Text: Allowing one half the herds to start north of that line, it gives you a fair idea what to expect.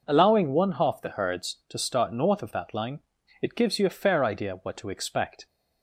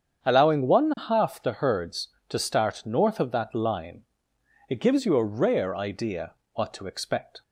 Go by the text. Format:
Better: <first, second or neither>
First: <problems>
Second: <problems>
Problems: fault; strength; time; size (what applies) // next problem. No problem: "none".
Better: first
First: none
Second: starts louder than the rest; strong; until 1.2 s; 7.5 dB // says "rare" for "fair"; at 5.2 s // pauses between "idea" and "what"; slight; at 6.3 s; 0.22 s long